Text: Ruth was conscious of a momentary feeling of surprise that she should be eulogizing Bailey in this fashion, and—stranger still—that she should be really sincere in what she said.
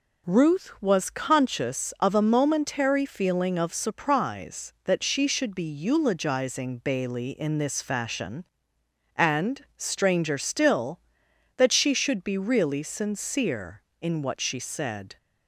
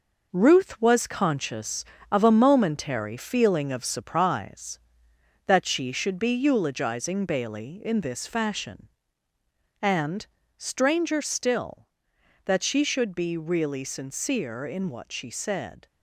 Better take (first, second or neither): first